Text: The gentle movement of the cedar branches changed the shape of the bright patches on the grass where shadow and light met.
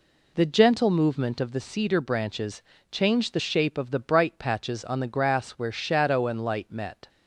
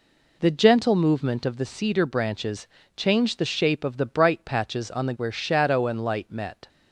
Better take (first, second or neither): first